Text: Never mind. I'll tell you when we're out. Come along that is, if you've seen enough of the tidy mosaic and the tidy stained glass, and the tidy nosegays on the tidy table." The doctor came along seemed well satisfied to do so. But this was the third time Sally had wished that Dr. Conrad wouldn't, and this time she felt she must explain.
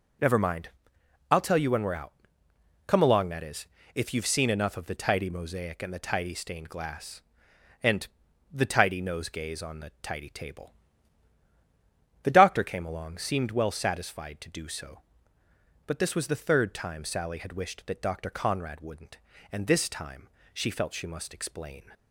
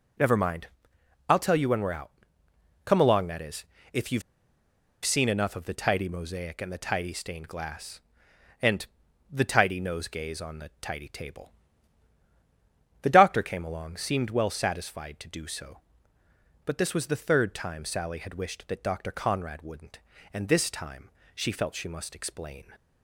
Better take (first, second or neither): first